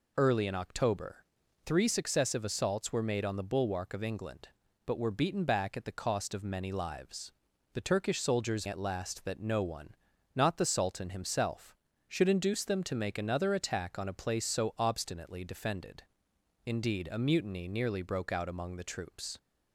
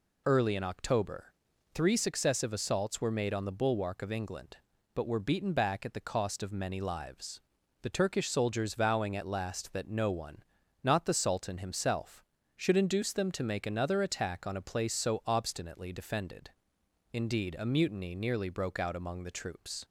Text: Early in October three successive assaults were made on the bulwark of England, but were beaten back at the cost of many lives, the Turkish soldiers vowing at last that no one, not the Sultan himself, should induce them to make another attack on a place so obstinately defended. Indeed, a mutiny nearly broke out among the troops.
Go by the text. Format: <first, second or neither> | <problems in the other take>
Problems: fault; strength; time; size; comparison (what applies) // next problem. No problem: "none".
second | pauses between "October" and "three"; noticeable; at 1.1 s; 0.46 s long; noticeable in the second // skips "vowing"; at 8.6 s